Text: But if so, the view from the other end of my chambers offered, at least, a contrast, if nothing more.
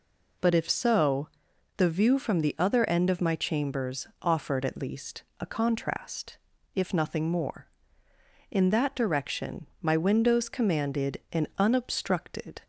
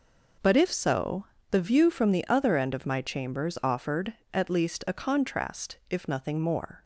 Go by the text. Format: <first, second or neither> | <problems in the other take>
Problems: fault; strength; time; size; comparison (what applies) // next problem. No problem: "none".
second | pauses between "chambers" and "offered"; slight; at 4.0 s; 0.16 s long // goes on to say "In that direction my windows commanded an unobstructed"; strong; from 8.5 s on; 4.1 s long